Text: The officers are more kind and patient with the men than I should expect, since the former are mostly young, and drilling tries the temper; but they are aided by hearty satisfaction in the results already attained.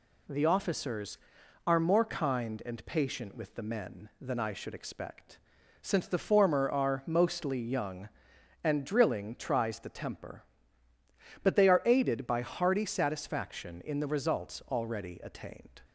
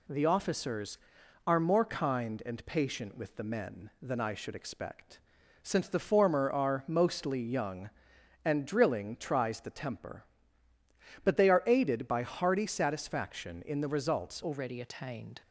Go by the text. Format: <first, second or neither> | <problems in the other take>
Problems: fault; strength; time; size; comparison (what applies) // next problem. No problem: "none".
first | changes voice at "already"; from 14.4 s on; 1.0 s long